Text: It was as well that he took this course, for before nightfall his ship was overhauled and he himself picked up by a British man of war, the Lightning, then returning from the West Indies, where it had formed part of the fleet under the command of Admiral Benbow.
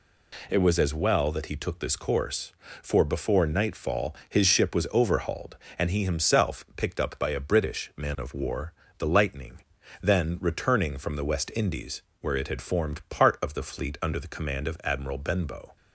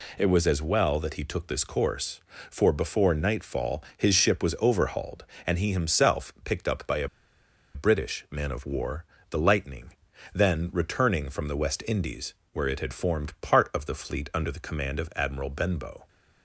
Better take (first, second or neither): first